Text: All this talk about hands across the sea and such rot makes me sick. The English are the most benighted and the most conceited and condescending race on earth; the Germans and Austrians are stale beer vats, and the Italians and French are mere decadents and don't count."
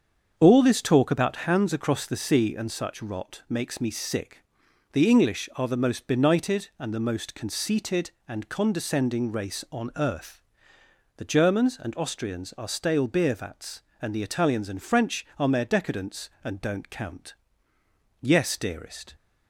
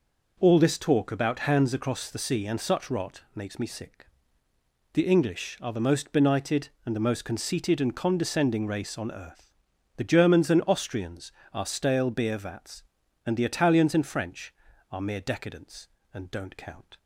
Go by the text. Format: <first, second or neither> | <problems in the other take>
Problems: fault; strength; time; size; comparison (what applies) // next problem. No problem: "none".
second | starts louder than the rest; strong; until 1.3 s; 7 dB // goes on to say "Yes dearest"; noticeable; from 18.1 s on; 0.96 s long